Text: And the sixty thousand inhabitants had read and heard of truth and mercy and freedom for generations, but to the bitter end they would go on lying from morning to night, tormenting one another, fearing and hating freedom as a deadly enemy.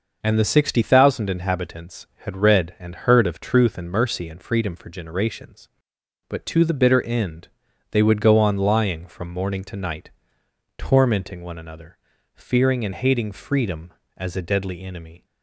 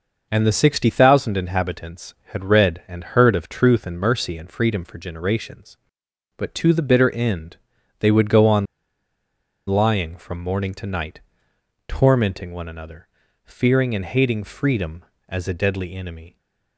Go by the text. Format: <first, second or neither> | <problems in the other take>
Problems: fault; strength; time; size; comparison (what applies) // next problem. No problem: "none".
first | pauses between "end" and "they"; at 7.5 s; 0.42 s long; also in the first // pauses between "on" and "lying"; at 8.6 s; 1.0 s long